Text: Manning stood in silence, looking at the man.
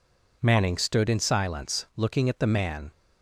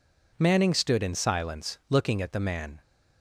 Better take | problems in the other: neither | none

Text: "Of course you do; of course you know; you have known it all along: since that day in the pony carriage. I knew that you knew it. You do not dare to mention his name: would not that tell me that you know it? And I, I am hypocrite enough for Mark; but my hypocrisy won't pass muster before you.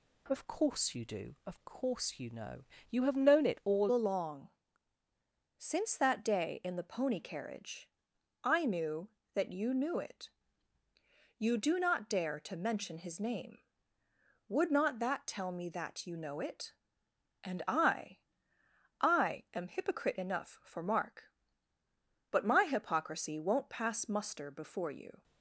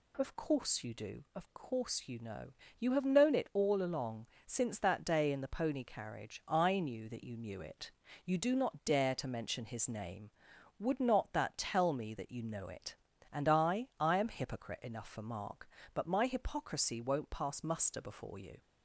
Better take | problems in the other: second | changes voice at "along"; from 3.9 s on; 21.3 s long

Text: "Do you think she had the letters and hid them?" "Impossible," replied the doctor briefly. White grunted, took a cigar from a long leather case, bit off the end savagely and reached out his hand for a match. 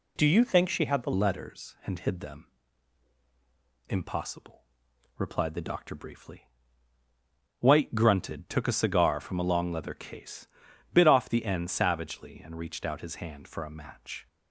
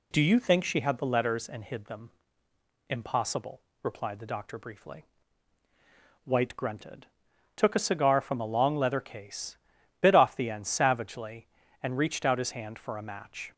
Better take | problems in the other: second | changes voice at "letters"; from 1.1 s on; 13.1 s long

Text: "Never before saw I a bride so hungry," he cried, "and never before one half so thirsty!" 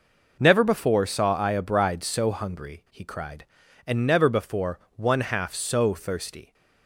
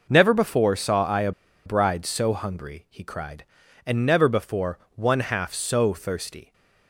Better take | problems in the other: first | pauses between "a" and "bride"; slight; at 1.3 s; 0.35 s long // pauses between "before" and "one"; slight; at 4.7 s; 0.16 s long; slight in the first

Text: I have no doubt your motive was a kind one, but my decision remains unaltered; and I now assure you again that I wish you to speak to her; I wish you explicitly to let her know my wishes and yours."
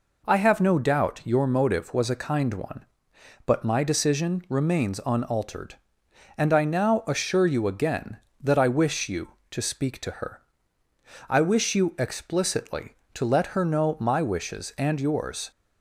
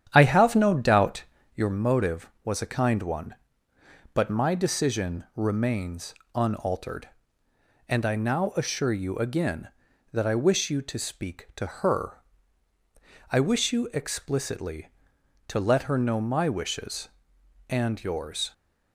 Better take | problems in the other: first | starts louder than the rest; strong; until 1.7 s; 9.5 dB // pauses between "doubt" and "your"; slight; at 1.2 s; 0.30 s long // pauses between "remains" and "unaltered"; slight; at 6.1 s; 0.20 s long

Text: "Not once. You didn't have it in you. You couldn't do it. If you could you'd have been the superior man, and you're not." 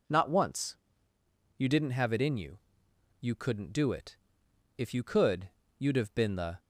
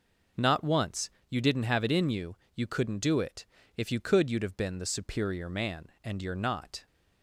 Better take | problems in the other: second | pauses between "could" and "you'd"; slight; at 5.4 s; 0.30 s long // stops before "superior man and you're not"; at 6.5 s

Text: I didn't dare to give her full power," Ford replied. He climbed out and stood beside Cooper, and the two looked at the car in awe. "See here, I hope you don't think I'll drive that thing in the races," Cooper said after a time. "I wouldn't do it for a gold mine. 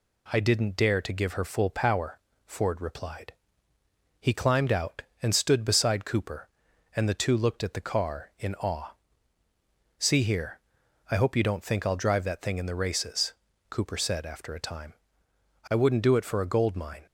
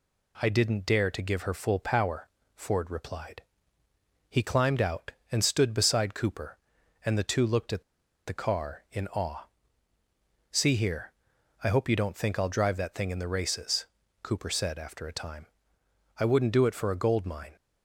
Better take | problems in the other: first | pauses between "at" and "the"; at 7.8 s; 0.44 s long

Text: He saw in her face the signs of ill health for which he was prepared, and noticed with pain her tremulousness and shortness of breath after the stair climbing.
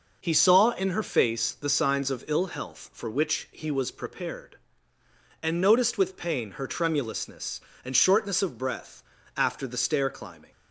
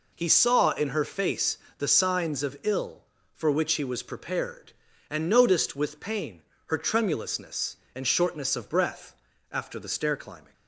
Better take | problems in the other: first | pauses between "face" and "the"; slight; at 1.5 s; 0.22 s long // skips "health"; at 3.1 s // pauses between "pain" and "her"; slight; at 6.4 s; 0.26 s long // pauses between "breath" and "after"; slight; at 9.1 s; 0.36 s long; slight in the first

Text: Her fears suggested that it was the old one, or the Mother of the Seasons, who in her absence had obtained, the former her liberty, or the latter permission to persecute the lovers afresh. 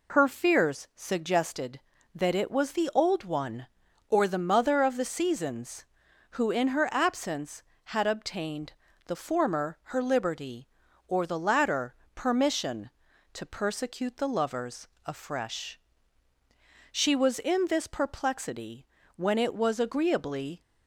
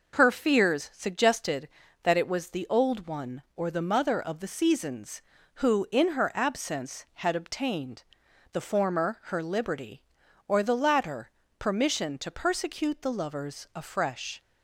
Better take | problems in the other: second | pauses between "latter" and "permission"; slight; at 11.9 s; 0.18 s long; slight in the second // pauses between "lovers" and "afresh"; slight; at 14.8 s; 0.16 s long // goes on to say "She was in this perplexity when it was agreeably"; strong; from 16.9 s on; 3.7 s long

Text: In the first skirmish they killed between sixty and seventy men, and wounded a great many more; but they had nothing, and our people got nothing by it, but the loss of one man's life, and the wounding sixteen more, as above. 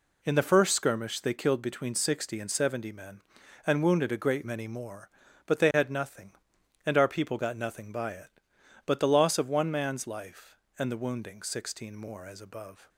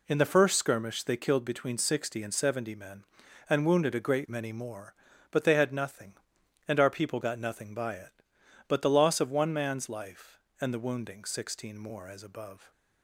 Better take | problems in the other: neither | none

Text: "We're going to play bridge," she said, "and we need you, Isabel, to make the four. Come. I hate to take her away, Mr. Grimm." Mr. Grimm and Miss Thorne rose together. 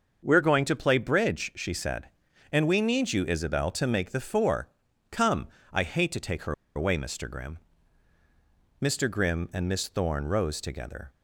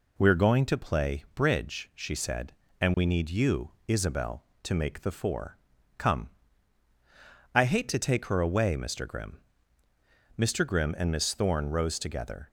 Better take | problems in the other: second | starts louder than the rest; until 1.2 s; 6.5 dB // pauses between "her" and "away"; slight; at 6.5 s; 0.22 s long

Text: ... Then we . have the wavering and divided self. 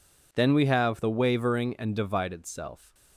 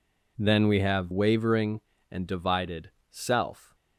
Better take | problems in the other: first | skips "the"; at 1.1 s // pauses between "divided" and "self"; slight; at 2.8 s; 0.22 s long

